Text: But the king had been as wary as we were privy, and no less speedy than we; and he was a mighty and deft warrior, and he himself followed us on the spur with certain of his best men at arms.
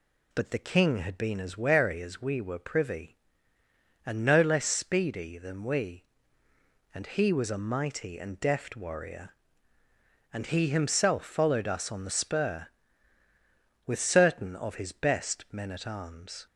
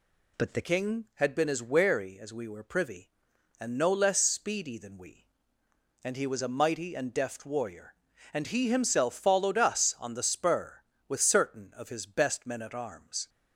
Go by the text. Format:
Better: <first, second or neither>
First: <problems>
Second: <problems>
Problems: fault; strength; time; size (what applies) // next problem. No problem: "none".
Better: first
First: none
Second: changes voice at "king"; from 0.6 s on; 12.6 s long